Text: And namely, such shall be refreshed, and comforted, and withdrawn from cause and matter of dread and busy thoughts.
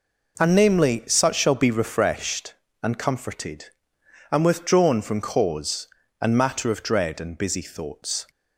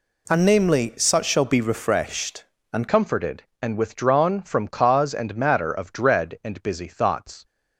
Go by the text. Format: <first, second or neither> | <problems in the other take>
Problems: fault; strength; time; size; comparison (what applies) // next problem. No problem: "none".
first | changes voice at "comforted"; from 2.8 s on; 4.6 s long